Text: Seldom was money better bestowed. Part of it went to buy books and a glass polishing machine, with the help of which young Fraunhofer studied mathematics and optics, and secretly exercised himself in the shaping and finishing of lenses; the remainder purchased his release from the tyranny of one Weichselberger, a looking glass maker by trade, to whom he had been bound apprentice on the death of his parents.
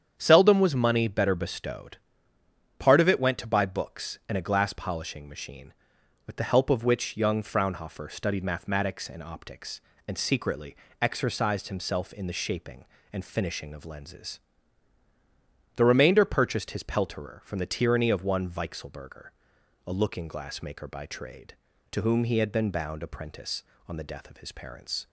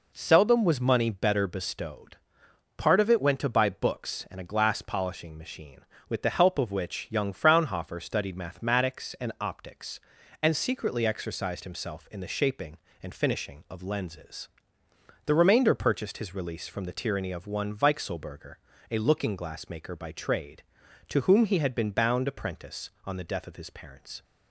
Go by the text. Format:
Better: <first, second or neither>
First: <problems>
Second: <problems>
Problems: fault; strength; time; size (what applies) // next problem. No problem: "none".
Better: second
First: starts louder than the rest; strong; until 1.1 s; 8.5 dB // pauses between "secretly" and "exercised"; slight; at 10.7 s; 0.28 s long // says "pelterer" for "release"; at 16.8 s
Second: none